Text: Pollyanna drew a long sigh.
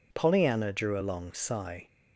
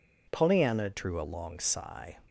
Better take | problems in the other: first | changes voice at "drew"; from 0.9 s on; 1.2 s long

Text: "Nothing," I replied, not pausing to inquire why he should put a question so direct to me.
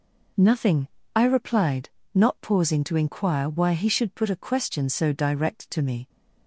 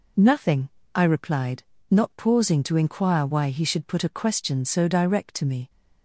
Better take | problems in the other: neither | none

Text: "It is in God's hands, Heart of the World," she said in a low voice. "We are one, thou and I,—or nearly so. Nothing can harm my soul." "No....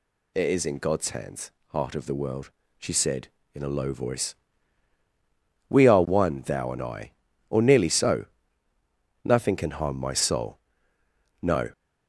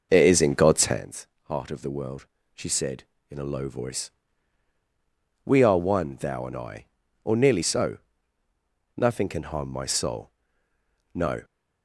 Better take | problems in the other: first | starts louder than the rest; noticeable; until 1.1 s; 5.5 dB

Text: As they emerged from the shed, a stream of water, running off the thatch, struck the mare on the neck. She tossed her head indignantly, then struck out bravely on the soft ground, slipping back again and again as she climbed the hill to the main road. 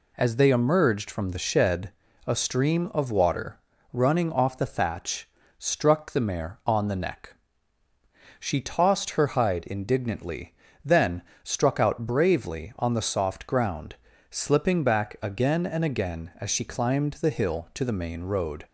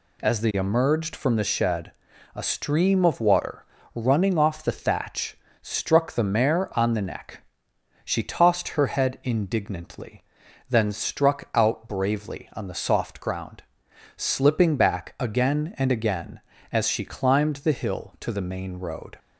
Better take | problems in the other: second | says "hide" for "head"; at 9.2 s // pauses between "then" and "struck"; slight; at 11.2 s; 0.22 s long

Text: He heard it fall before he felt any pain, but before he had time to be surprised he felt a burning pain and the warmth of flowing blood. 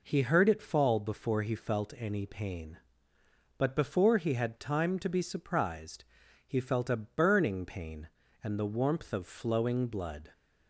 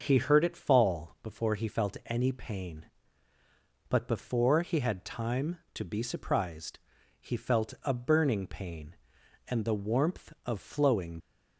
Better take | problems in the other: first | starts louder than the rest; until 1.0 s; 6 dB // pauses between "surprised" and "he"; at 6.7 s; 0.42 s long; also in the first // stops before "blood"; at 11.1 s

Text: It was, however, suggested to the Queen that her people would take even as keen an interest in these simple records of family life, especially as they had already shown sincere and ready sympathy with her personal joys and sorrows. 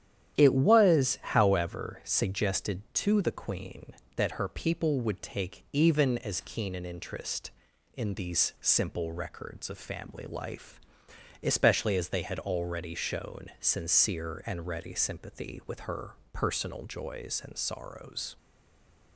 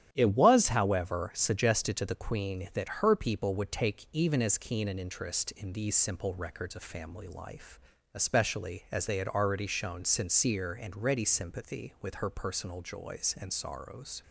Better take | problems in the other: second | starts louder than the rest; strong; until 1.4 s; 10.5 dB; strong in the second // pauses between "her" and "personal"; slight; at 16.1 s; 0.18 s long // stays silent after the last word; slight; from 18.3 s on; 0.8 s long

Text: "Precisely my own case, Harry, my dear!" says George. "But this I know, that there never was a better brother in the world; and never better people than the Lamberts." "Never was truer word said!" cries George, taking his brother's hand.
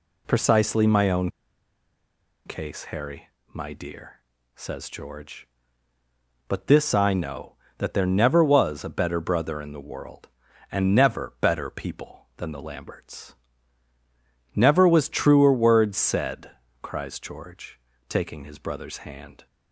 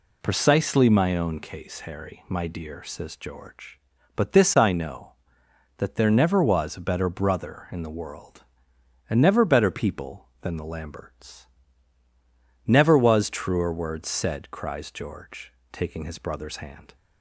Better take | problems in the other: second | pauses between "own" and "case"; at 1.2 s; 1.1 s long

